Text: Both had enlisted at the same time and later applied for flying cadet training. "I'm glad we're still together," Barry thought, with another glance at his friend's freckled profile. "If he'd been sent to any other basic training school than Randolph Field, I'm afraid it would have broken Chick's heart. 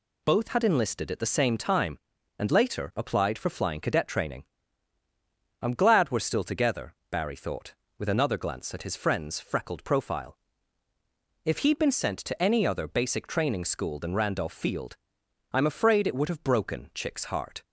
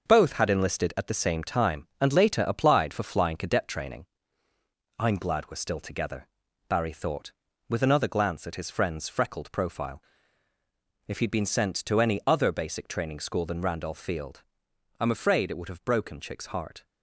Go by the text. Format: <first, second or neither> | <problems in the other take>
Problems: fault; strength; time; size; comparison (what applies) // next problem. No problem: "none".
first | gets quieter; throughout; 6.5 dB